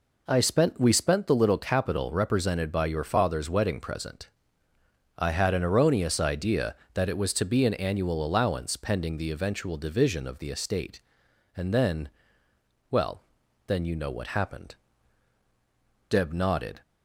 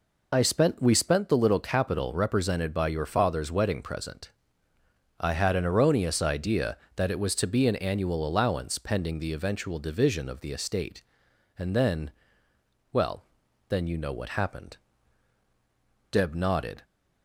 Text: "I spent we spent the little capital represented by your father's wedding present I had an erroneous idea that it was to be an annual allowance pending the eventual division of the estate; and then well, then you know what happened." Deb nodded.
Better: first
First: pauses between "present" and "I"; noticeable; at 4.2 s; 0.88 s long // pauses between "then" and "well"; noticeable; at 12.0 s; 0.82 s long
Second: loses the start of "I"; at 0.3 s; 30 ms // pauses between "present" and "I"; noticeable; at 4.3 s; 0.88 s long // pauses between "then" and "well"; noticeable; at 12.0 s; 0.82 s long

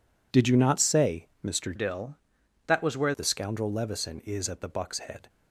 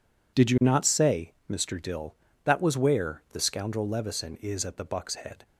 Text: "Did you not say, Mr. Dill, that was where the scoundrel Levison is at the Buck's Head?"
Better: second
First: changes voice from "Dill" to "where"; from 1.7 to 3.1 s; 1.4 s long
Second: none

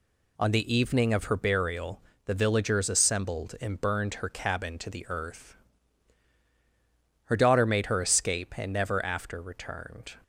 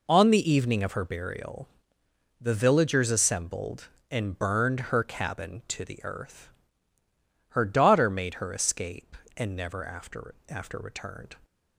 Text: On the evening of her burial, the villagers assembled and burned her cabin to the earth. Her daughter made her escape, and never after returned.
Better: first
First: none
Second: says "after" twice; at 10.4 s

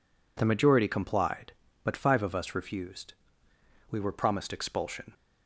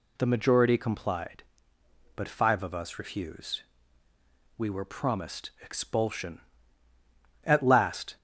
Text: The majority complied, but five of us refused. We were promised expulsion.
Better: first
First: none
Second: goes on to say "At last"; noticeable; from 7.4 s on; 0.72 s long

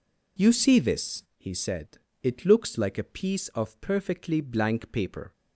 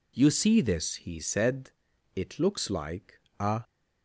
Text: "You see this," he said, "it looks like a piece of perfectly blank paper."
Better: first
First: none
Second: pauses between "like" and "a"; slight; at 3.1 s; 0.22 s long // stops before "piece of perfectly blank paper"; at 3.6 s

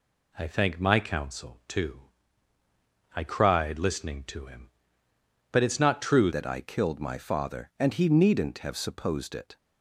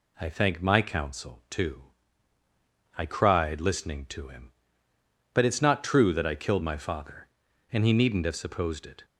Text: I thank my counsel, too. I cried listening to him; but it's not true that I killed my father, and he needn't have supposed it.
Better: second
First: changes voice at "that"; from 6.3 s on; 3.2 s long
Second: none

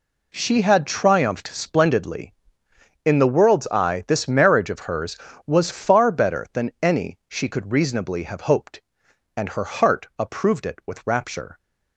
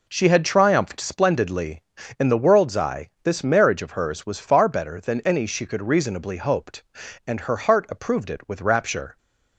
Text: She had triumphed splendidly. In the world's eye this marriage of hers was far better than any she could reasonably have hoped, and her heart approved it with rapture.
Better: first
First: none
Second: pauses between "eye" and "this"; slight; at 3.0 s; 0.16 s long // skips "have"; at 6.3 s

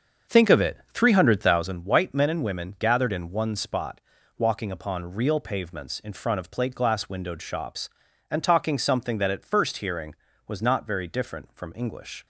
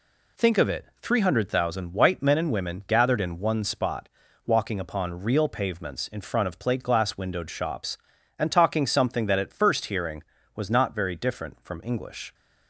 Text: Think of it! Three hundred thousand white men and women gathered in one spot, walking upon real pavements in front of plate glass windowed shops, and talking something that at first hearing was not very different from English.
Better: second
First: starts louder than the rest; until 1.8 s; 7 dB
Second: none

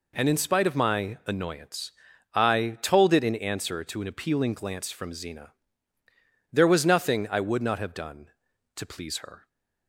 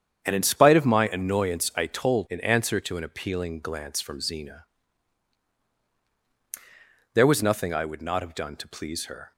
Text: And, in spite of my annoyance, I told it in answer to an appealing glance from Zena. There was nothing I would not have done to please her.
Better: first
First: none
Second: starts louder than the rest; strong; until 1.2 s; 8.5 dB // skips "it"; at 2.2 s

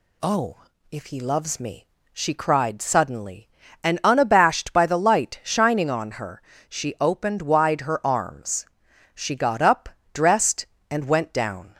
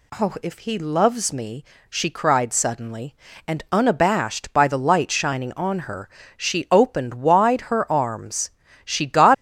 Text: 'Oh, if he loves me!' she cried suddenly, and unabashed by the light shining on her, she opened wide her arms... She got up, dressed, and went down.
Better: first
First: none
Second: stops before "up dressed and went down"; at 9.3 s

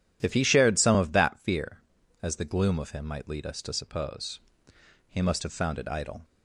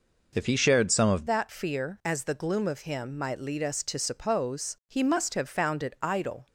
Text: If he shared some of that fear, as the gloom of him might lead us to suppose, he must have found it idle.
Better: first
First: none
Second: changes voice at "that"; from 1.2 s on; 5.2 s long

